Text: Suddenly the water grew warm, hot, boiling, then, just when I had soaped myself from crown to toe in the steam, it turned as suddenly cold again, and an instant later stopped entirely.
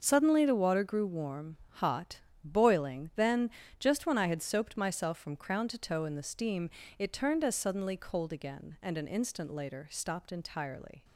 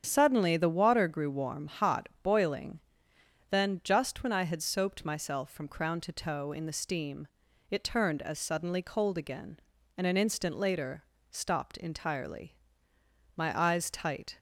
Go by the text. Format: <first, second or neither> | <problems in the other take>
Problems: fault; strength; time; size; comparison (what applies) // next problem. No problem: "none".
first | starts louder than the rest; strong; until 1.0 s; 7.5 dB; also in the first // pauses between "later" and "stopped"; slight; at 11.0 s; 0.26 s long // goes on to say "My eyes tight"; noticeable; from 13.3 s on; 1.0 s long